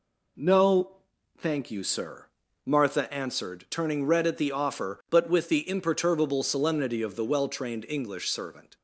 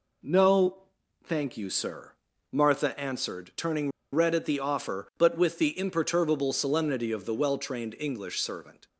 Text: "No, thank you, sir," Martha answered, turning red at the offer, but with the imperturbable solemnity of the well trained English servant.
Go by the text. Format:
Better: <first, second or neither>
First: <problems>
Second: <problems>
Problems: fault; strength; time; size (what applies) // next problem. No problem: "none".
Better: first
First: none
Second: pauses between "turning" and "red"; slight; at 3.9 s; 0.22 s long